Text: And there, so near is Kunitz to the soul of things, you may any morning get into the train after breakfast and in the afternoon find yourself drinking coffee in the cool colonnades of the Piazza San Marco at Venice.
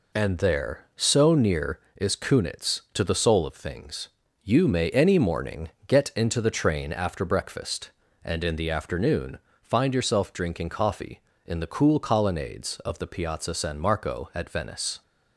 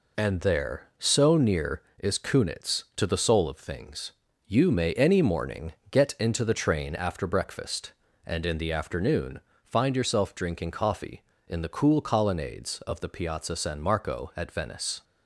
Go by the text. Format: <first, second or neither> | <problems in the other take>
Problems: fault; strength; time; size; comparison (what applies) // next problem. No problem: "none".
neither | pauses between "morning" and "get"; slight; the same in both // pauses between "afternoon" and "find"; slight; the same in both